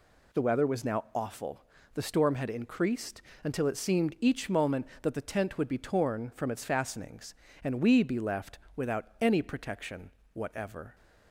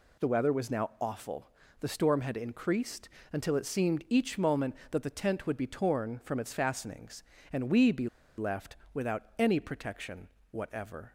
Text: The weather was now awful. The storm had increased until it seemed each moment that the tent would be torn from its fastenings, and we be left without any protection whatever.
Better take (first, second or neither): first